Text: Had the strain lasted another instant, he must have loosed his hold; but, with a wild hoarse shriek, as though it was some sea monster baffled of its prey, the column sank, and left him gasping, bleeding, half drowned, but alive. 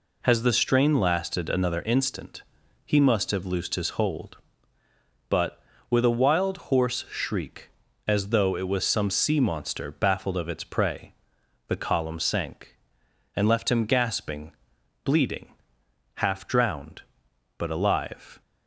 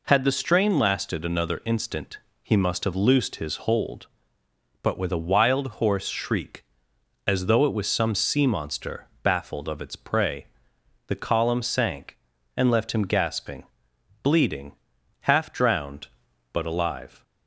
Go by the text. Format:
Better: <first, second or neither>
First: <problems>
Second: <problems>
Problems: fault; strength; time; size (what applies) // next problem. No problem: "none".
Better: second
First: says "Has" for "Had"; at 0.2 s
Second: none